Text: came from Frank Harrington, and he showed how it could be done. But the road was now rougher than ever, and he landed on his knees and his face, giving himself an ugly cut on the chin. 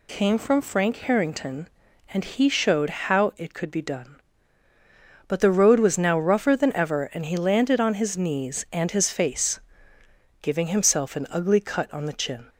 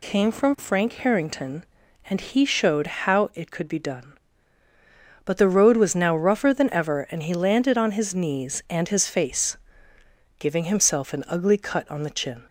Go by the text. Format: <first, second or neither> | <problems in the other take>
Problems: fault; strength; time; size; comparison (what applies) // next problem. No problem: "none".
neither | none